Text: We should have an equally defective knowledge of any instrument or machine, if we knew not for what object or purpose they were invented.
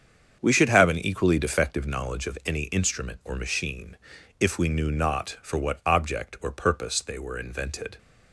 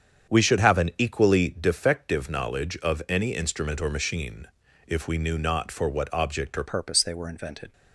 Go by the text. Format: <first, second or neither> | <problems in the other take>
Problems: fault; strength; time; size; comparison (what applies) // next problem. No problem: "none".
first | starts louder than the rest; strong; until 1.3 s; 8 dB; strong in the first // changes voice at "purpose"; from 6.6 s on; 1.1 s long